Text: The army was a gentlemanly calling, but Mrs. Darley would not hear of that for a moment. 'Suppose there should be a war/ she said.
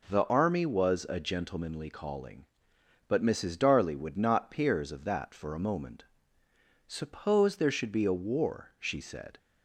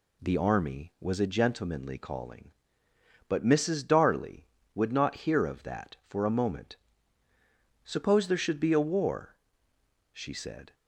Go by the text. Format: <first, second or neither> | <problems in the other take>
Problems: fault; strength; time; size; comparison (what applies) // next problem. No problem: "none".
second | says "peers" for "hear"; at 4.4 s